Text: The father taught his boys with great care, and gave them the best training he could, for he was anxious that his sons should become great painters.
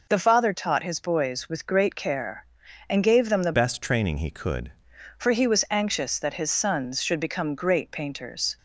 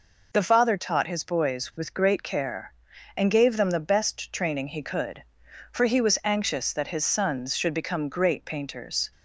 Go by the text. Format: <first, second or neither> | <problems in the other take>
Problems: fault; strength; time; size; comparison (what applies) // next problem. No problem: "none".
second | changes voice from "best" to "could"; from 3.5 to 4.7 s; 1.2 s long